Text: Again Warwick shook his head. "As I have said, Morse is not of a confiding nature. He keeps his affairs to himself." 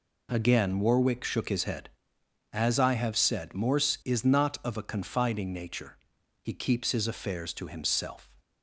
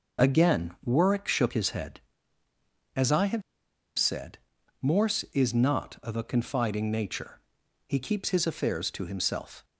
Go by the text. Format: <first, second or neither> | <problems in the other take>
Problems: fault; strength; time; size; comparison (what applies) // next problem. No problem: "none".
first | pauses between "have" and "said"; noticeable; at 3.4 s; 0.55 s long